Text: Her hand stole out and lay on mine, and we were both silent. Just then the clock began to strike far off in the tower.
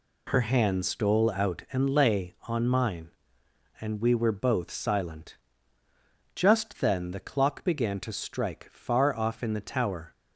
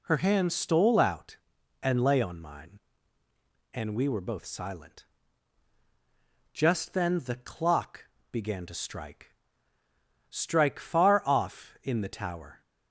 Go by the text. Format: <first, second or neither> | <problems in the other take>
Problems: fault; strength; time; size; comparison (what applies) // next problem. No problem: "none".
first | pauses between "clock" and "began"; slight; at 8.0 s; 0.24 s long // says "strike" twice; at 10.3 s